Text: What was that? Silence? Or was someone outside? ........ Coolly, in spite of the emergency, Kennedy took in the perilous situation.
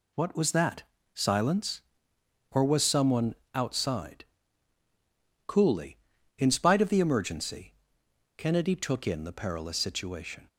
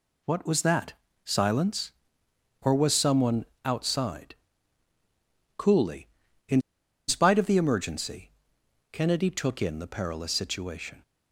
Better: first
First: pauses between "someone" and "outside"; slight; at 3.3 s; 0.22 s long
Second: pauses between "someone" and "outside"; slight; at 3.4 s; 0.22 s long // pauses between "in" and "spite"; noticeable; at 6.6 s; 0.46 s long

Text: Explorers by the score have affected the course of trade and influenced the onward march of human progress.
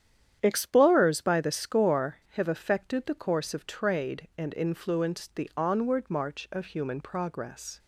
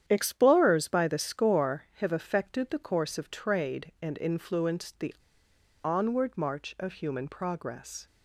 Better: first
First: starts louder than the rest; strong; until 1.4 s; 9.5 dB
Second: starts louder than the rest; strong; until 1.0 s; 9.5 dB // pauses between "the" and "onward"; noticeable; at 5.1 s; 0.71 s long

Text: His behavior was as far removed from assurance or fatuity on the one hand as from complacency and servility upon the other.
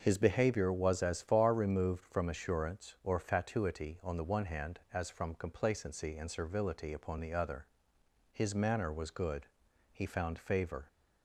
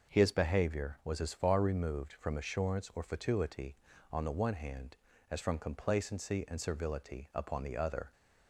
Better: second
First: starts louder than the rest; until 1.0 s; 6 dB // goes on to say "His manner was good he found favor"; strong; from 8.3 s on; 2.5 s long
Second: none

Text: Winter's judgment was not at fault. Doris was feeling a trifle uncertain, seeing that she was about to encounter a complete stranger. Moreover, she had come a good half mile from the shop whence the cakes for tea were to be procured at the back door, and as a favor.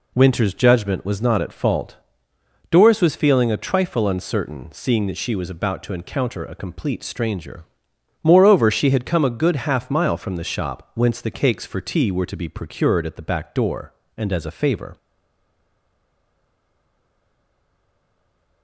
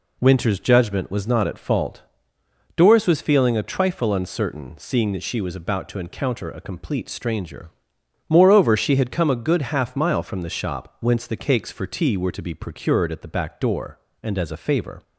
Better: second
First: stays silent after the last word; strong; from 14.9 s on; 3.7 s long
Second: none

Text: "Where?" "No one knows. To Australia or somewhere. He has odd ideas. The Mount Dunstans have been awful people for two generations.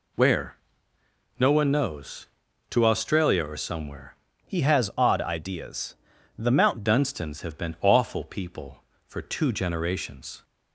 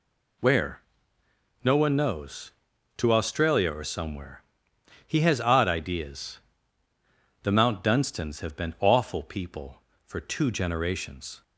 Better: second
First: changes voice from "He" to "Mount"; from 4.4 to 6.8 s; 2.4 s long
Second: none

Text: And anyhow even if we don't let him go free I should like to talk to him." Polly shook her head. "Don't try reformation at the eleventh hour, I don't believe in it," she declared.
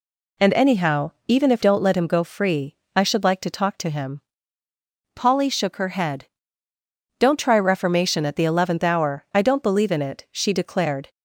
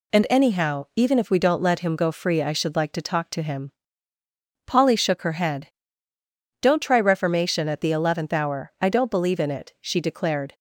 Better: second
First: pauses between "anyhow" and "even"; slight; at 1.1 s; 0.16 s long // skips "we"; at 1.6 s // pauses between "free" and "I"; slight; at 2.7 s; 0.20 s long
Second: none

